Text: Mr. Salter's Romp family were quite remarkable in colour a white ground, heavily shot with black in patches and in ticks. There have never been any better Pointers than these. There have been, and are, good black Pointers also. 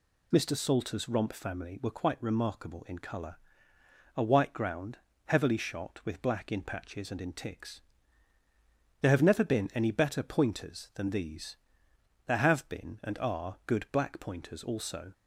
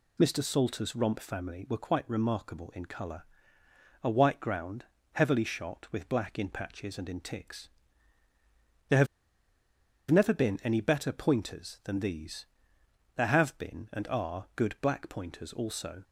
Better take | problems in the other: first | pauses between "colour" and "a"; noticeable; at 3.2 s; 0.80 s long; noticeable in the first // pauses between "have" and "never"; at 9.0 s; 1.0 s long

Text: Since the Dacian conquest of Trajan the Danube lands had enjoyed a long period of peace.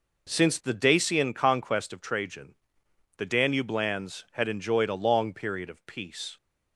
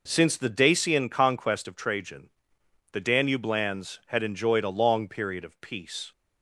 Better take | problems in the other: neither | pauses between "Trajan" and "the"; noticeable; the same in both

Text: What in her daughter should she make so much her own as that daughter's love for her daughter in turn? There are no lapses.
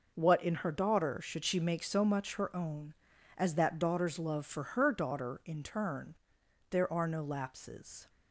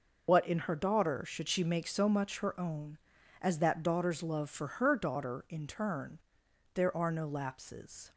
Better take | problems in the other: first | loses the start of "What"; at 0.2 s; 95 ms

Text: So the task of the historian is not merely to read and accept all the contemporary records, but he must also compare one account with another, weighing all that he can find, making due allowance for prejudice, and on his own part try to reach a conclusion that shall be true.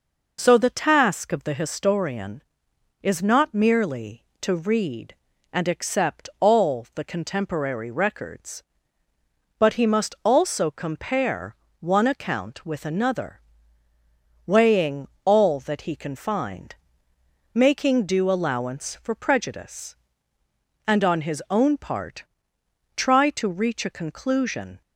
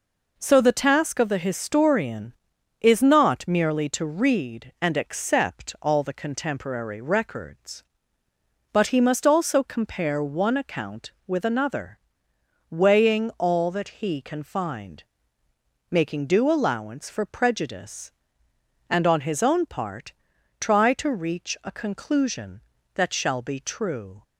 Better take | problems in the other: second | pauses between "compare" and "one"; slight; at 11.5 s; 0.24 s long // pauses between "weighing" and "all"; slight; at 15.0 s; 0.18 s long // pauses between "part" and "try"; noticeable; at 22.2 s; 0.70 s long; noticeable in the second // stops before "that shall be true"; at 24.8 s

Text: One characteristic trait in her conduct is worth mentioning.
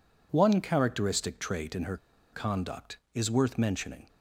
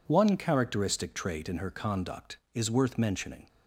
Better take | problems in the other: second | pauses between "her" and "conduct"; at 1.9 s; 0.36 s long

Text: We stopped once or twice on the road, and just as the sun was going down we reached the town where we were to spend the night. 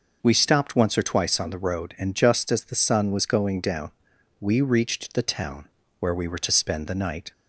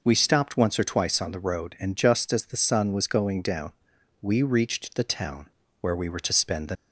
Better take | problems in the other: first | pauses between "down" and "we"; noticeable; at 3.7 s; 0.50 s long; noticeable in the first // pauses between "town" and "where"; slight; at 5.4 s; 0.32 s long; slight in the first // stops before "night"; at 6.7 s

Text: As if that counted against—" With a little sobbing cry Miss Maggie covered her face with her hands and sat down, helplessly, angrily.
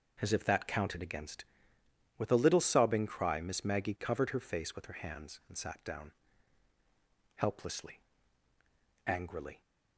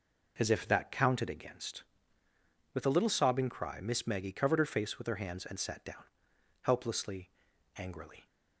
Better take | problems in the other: neither | none

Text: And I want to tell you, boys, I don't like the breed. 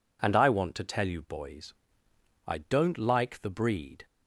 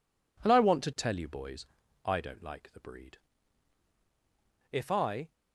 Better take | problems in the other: first | goes on to say "If I"; from 4.7 s on; 0.60 s long

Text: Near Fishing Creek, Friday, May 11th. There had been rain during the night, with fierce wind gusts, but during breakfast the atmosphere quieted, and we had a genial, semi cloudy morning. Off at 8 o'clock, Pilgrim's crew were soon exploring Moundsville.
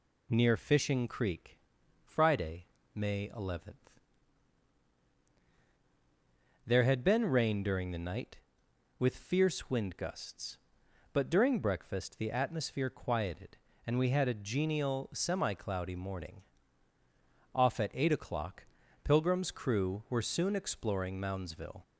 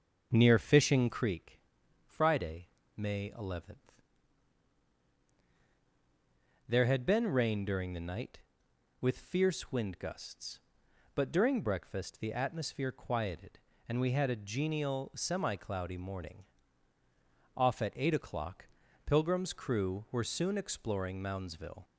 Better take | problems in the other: first | starts louder than the rest; until 1.3 s; 7 dB

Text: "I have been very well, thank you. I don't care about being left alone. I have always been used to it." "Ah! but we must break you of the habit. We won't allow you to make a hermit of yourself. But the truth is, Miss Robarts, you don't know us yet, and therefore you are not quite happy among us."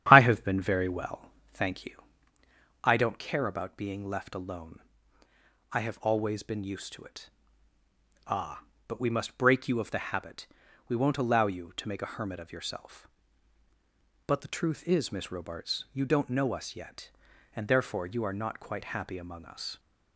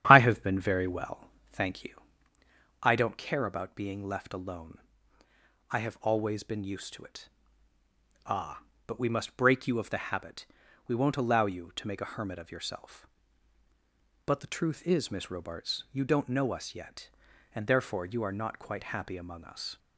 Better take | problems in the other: neither | starts louder than the rest; strong; the same in both

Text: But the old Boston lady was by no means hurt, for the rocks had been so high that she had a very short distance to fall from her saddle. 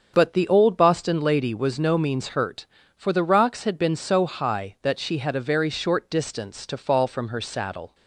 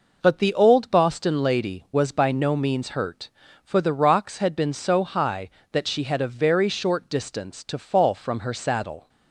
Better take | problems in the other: second | starts louder than the rest; until 1.1 s; 7 dB // skips "by"; at 1.7 s

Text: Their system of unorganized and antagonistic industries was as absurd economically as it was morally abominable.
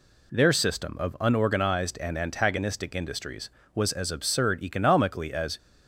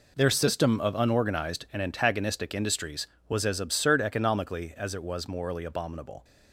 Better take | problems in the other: second | stops before "it was morally abominable"; at 5.5 s

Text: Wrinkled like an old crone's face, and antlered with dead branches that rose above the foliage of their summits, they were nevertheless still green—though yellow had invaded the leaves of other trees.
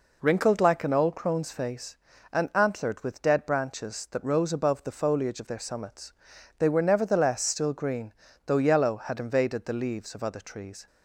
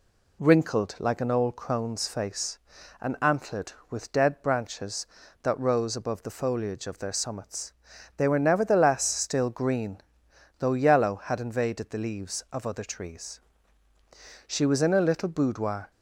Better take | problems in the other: first | goes on to say "She was in a little boudoir"; from 14.4 s on; 1.4 s long

